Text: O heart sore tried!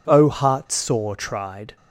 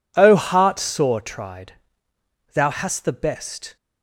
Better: first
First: none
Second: goes on to say "thou hast the best"; noticeable; from 2.5 s on; 1.2 s long

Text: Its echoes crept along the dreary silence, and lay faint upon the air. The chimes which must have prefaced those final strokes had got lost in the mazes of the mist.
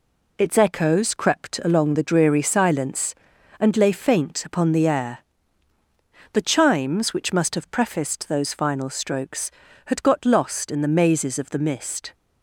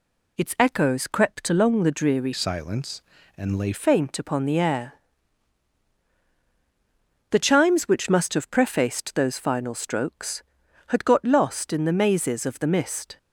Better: first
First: none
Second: changes voice from "silence" to "lay"; from 2.3 to 3.7 s; 1.4 s long

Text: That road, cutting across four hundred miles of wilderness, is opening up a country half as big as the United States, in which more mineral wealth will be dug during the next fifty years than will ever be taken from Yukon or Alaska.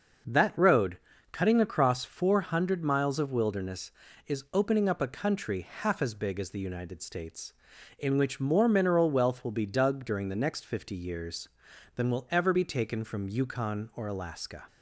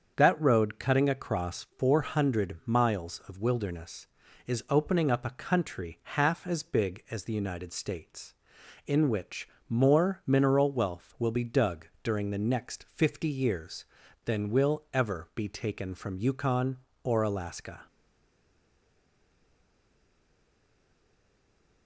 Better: first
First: starts louder than the rest; until 1.6 s; 6.5 dB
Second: starts louder than the rest; strong; until 1.1 s; 7.5 dB // pauses between "which" and "more"; slight; at 9.4 s; 0.20 s long // pauses between "dug" and "during"; slight; at 11.8 s; 0.18 s long // stays silent after the last word; strong; from 17.8 s on; 4.0 s long

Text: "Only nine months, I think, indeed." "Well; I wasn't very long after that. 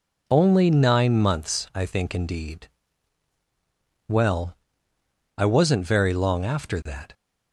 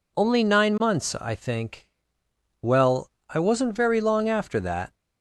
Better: first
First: none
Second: skips "indeed"; at 2.2 s

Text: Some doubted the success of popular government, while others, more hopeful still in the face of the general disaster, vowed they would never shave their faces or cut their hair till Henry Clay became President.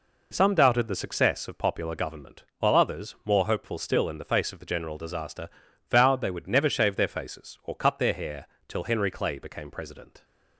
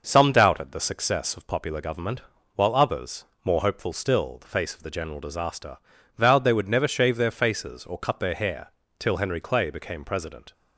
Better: first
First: pauses between "hair" and "till"; slight; at 8.4 s; 0.20 s long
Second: skips "in"; at 4.3 s // pauses between "hair" and "till"; slight; at 8.6 s; 0.30 s long

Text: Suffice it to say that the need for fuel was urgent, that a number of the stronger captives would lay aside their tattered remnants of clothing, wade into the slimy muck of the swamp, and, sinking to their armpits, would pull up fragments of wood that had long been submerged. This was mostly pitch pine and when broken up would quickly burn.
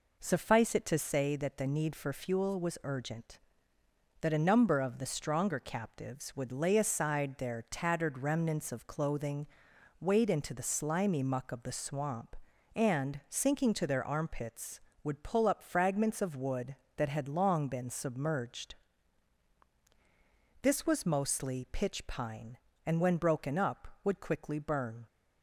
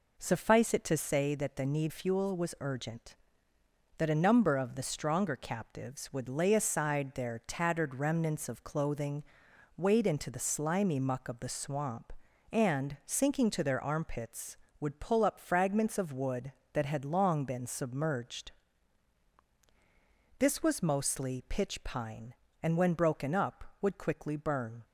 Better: first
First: none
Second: skips "for"; at 1.9 s

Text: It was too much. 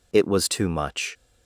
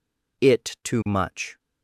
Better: first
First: none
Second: skips "was"; at 0.7 s

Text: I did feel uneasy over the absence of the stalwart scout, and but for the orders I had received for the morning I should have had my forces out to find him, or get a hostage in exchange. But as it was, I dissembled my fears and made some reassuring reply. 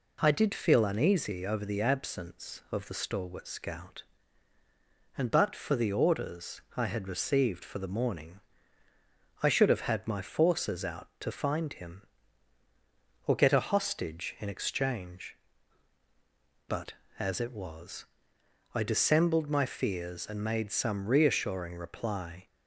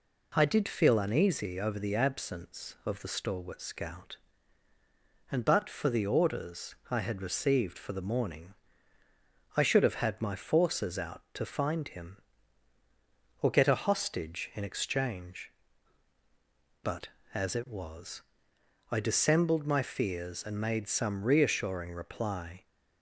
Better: neither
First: pauses between "orders" and "I"; slight; at 6.5 s; 0.16 s long // pauses between "morning" and "I"; at 8.4 s; 1.0 s long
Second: pauses between "orders" and "I"; slight; at 6.7 s; 0.16 s long // pauses between "morning" and "I"; at 8.5 s; 1.0 s long

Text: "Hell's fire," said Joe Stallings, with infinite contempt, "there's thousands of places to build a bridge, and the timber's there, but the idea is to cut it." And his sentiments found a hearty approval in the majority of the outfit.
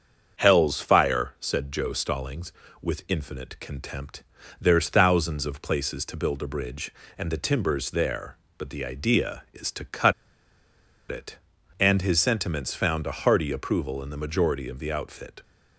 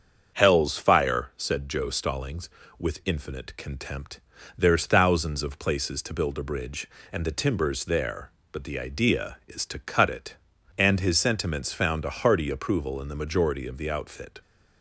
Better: second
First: starts louder than the rest; strong; until 1.4 s; 7 dB // pauses between "cut" and "it"; noticeable; at 10.1 s; 0.97 s long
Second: starts louder than the rest; strong; until 1.4 s; 7 dB

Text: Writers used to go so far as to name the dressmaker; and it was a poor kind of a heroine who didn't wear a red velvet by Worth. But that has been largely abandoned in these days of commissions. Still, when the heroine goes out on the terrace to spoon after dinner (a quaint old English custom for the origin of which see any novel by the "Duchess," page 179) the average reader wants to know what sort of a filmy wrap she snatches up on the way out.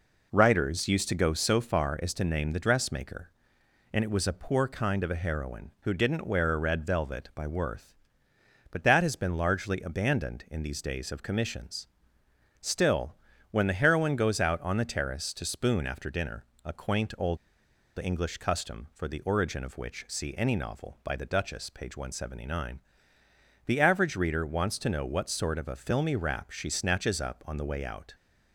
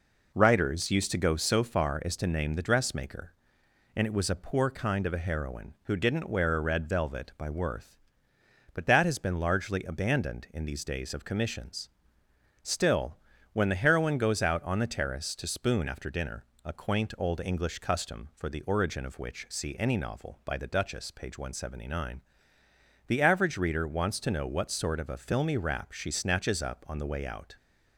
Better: second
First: pauses between "old" and "English"; noticeable; at 17.3 s; 0.60 s long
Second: none

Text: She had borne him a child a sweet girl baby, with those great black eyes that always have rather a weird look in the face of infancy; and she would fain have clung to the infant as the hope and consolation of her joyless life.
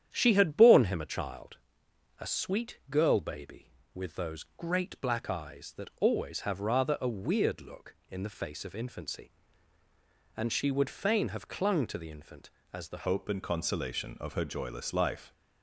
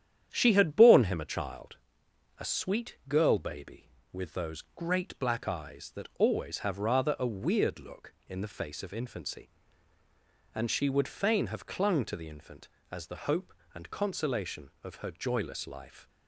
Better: second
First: starts louder than the rest; strong; until 1.1 s; 9.5 dB // pauses between "child" and "a"; noticeable; at 1.5 s; 0.64 s long // changes voice at "hope"; from 13.0 s on; 2.3 s long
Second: starts louder than the rest; strong; until 1.3 s; 9.5 dB // pauses between "child" and "a"; noticeable; at 1.7 s; 0.64 s long

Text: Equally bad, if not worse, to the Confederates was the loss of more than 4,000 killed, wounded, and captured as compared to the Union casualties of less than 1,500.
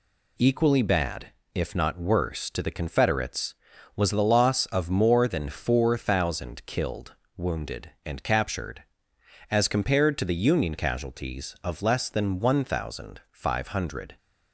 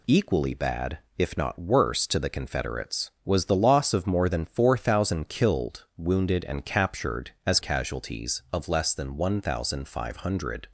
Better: first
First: none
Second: skips "compared to the Union"; at 7.6 s

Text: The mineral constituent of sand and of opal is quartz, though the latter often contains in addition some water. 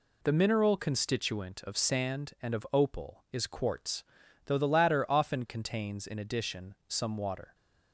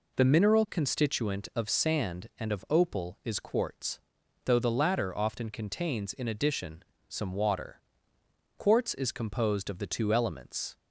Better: first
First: pauses between "addition" and "some"; slight; at 6.7 s; 0.16 s long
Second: pauses between "addition" and "some"; slight; at 6.8 s; 0.24 s long // goes on to say "Quartz is composed of the two elements"; strong; from 8.5 s on; 2.2 s long

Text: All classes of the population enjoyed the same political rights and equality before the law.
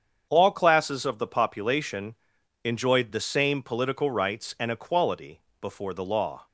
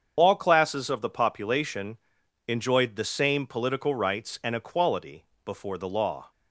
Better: first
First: starts louder than the rest; strong; until 1.3 s; 7.5 dB // pauses between "population" and "enjoyed"; noticeable; at 2.1 s; 0.51 s long // pauses between "equality" and "before"; slight; at 5.3 s; 0.22 s long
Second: loses the start of "All"; at 0.1 s; 35 ms // starts louder than the rest; strong; until 1.1 s; 7.5 dB // pauses between "population" and "enjoyed"; noticeable; at 1.9 s; 0.52 s long // pauses between "equality" and "before"; slight; at 5.2 s; 0.22 s long

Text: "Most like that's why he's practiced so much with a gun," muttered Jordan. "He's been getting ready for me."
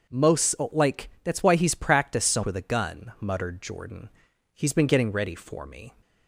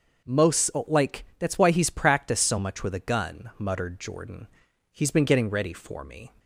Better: second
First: pauses between "Most" and "like"; slight; at 0.5 s; 0.16 s long // skips "much"; at 2.4 s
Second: pauses between "Most" and "like"; slight; at 0.7 s; 0.16 s long

